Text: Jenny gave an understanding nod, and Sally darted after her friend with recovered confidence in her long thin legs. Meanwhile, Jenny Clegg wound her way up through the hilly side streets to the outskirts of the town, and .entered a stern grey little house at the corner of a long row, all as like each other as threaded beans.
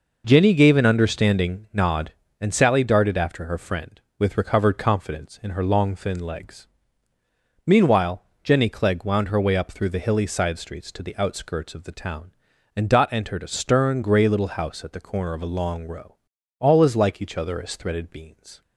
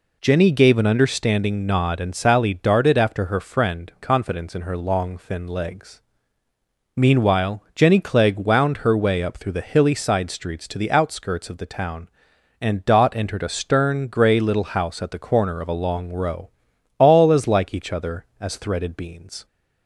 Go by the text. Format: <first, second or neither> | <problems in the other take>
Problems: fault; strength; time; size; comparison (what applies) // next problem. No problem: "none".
first | skips "with recovered"; at 3.9 s